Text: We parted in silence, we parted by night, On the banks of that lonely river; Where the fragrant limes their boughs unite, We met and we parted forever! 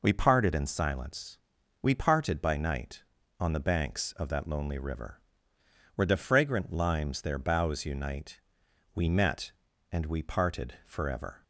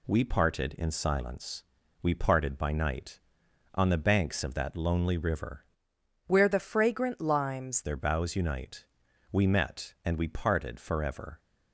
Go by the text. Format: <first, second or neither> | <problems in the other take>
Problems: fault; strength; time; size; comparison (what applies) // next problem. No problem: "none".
first | changes voice from "Where" to "limes"; from 6.2 to 7.8 s; 1.6 s long